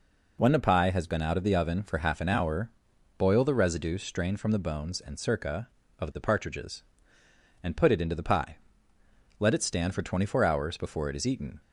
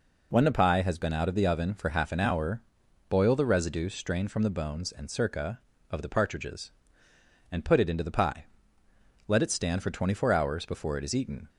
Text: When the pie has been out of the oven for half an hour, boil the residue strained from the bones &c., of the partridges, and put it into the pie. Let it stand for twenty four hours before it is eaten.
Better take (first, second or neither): neither